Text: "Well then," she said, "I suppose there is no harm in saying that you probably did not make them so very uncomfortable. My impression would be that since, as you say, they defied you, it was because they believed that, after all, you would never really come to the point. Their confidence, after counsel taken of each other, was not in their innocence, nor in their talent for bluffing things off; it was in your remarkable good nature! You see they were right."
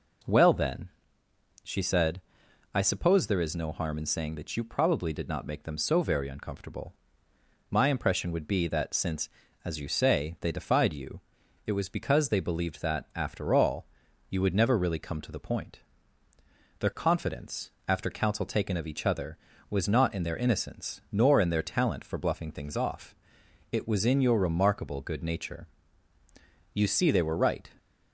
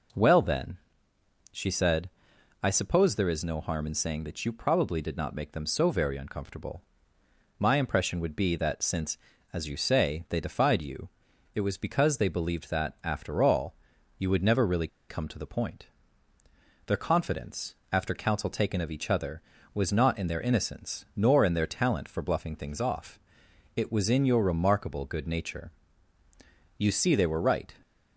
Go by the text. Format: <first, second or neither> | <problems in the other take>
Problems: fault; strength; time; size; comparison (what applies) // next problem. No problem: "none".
first | pauses between "really" and "come"; slight; at 14.8 s; 0.21 s long